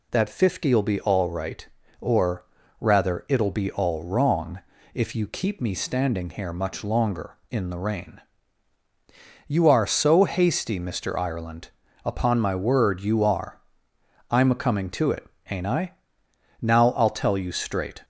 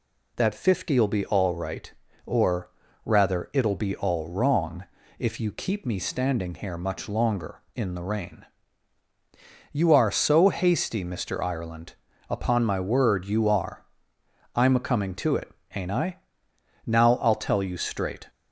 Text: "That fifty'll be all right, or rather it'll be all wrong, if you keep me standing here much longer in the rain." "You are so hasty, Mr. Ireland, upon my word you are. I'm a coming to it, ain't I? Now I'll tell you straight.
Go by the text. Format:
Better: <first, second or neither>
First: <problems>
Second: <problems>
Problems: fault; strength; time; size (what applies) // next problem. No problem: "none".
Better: neither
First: pauses between "or" and "rather"; slight; at 2.4 s; 0.34 s long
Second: pauses between "or" and "rather"; slight; at 2.7 s; 0.33 s long